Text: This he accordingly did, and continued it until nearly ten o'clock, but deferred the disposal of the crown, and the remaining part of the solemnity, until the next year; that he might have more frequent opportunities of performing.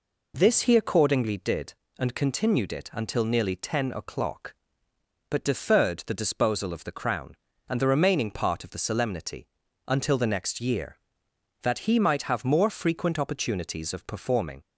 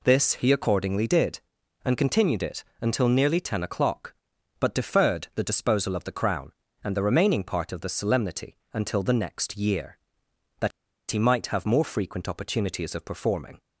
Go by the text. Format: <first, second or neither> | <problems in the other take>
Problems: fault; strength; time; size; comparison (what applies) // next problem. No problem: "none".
first | pauses between "it" and "until"; slight; at 2.6 s; 0.18 s long // pauses between "that" and "he"; at 10.7 s; 0.40 s long